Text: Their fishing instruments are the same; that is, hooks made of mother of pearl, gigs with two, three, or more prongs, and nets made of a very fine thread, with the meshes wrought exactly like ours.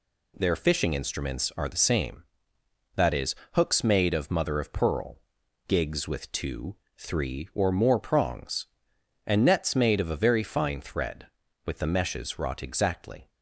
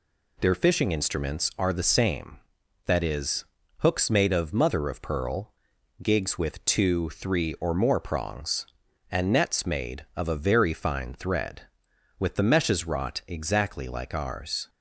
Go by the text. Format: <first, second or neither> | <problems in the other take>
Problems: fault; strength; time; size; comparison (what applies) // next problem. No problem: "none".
second | stops before "like ours"; at 13.2 s